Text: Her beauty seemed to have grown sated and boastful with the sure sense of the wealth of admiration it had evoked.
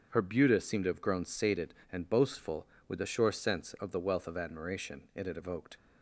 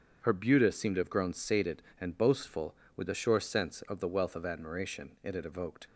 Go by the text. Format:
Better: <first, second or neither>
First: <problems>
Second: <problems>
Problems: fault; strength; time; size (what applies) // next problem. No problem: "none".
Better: neither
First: starts louder than the rest; until 1.1 s; 7 dB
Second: starts louder than the rest; strong; until 1.2 s; 7.5 dB